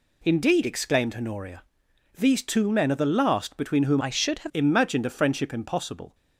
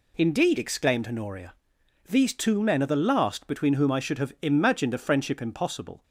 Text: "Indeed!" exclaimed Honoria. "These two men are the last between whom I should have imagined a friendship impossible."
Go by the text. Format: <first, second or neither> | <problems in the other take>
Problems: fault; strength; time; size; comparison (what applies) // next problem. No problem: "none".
second | changes voice from "I" to "have"; from 3.9 to 4.5 s; 0.6 s long